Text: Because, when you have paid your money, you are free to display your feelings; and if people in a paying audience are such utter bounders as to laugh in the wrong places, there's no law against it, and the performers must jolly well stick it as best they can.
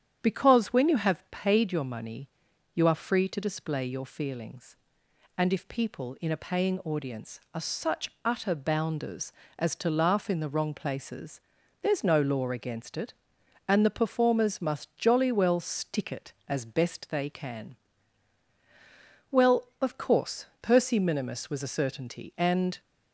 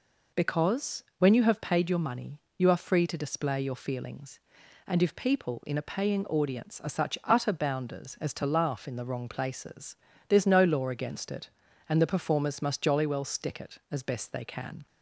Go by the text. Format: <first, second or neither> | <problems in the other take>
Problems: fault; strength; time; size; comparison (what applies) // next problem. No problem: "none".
second | starts louder than the rest; strong; until 1.2 s; 9 dB // goes on to say "Well of course Percy minimus was a certainty and"; strong; from 19.2 s on; 3.5 s long